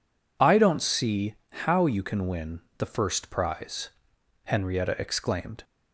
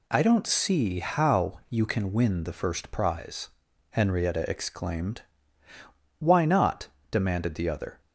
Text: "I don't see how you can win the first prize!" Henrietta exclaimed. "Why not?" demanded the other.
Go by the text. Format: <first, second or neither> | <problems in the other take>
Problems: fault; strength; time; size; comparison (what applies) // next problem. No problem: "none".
second | pauses between "see" and "how"; slight; at 1.3 s; 0.18 s long // pauses between "win" and "the"; slight; at 2.6 s; 0.18 s long // stops before "Why not demanded the other"; at 5.6 s